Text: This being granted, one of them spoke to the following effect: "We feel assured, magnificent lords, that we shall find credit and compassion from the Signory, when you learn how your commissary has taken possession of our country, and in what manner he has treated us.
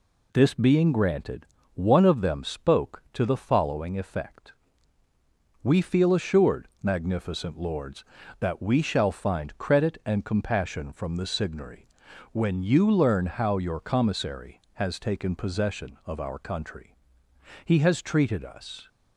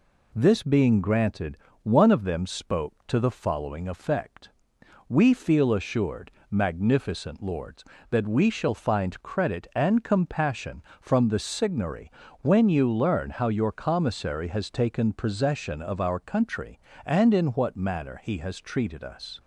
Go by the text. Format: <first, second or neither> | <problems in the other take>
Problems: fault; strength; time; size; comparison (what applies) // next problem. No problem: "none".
second | skips "and in what manner"; at 17.2 s